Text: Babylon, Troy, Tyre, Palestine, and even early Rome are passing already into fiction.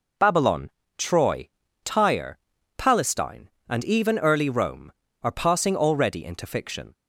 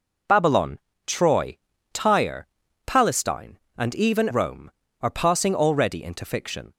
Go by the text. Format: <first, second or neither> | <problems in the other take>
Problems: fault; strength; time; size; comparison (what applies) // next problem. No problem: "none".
first | skips "early"; at 4.2 s